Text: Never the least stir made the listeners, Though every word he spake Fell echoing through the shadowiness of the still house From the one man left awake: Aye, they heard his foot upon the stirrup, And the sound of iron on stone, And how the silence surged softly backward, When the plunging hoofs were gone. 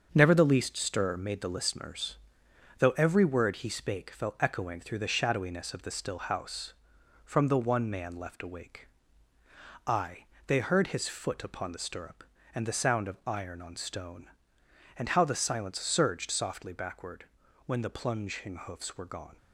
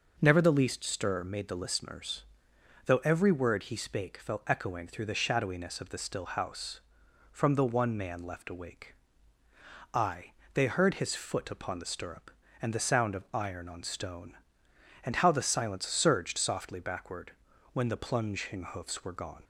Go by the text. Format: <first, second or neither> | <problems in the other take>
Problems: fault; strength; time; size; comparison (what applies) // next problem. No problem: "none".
second | gets quieter; throughout; 6.5 dB